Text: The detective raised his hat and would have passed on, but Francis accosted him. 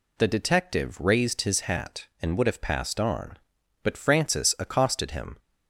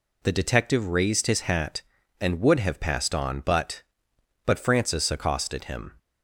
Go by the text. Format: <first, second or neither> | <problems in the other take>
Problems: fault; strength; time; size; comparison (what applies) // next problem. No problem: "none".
first | says "but" twice; at 4.4 s